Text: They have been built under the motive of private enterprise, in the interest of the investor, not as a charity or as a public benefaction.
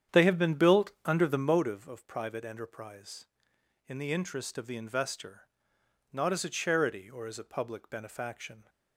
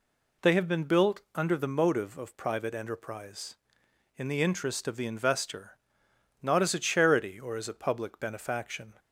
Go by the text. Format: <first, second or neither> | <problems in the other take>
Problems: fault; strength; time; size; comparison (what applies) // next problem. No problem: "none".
second | starts louder than the rest; strong; until 1.8 s; 9 dB